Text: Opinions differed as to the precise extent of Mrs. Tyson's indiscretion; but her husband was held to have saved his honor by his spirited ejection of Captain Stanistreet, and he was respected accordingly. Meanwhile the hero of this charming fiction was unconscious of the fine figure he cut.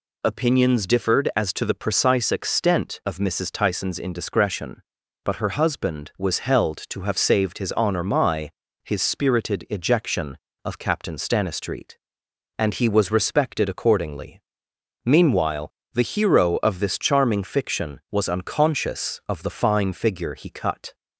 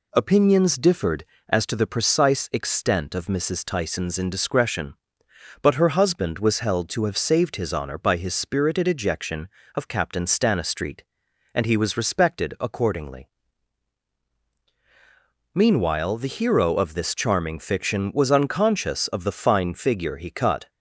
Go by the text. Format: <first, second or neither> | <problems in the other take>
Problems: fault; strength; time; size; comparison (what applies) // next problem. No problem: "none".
second | says "my" for "by"; at 8.0 s // pauses between "Meanwhile" and "the"; slight; at 15.7 s; 0.22 s long